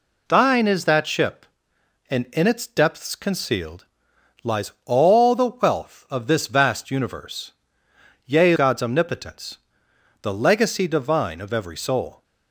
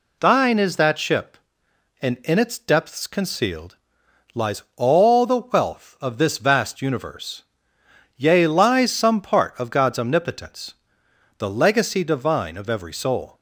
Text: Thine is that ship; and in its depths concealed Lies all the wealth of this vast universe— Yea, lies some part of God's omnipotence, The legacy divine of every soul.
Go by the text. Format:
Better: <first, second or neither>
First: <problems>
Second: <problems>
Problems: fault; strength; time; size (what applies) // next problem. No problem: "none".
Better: second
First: pauses between "concealed" and "Lies"; noticeable; at 3.8 s; 0.58 s long // skips "lies some part of"; at 8.5 s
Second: pauses between "concealed" and "Lies"; noticeable; at 3.7 s; 0.58 s long